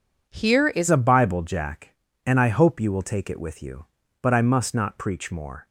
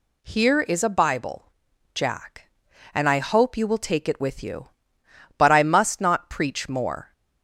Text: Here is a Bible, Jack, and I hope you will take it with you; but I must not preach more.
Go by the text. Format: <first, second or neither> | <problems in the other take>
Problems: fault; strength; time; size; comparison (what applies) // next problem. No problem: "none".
second | changes voice at "a"; from 0.8 s on; 4.8 s long